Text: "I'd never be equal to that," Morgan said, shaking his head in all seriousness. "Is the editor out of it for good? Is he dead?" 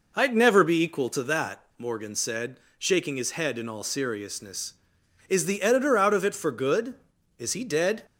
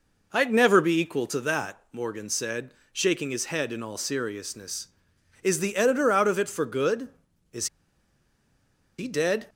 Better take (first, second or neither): first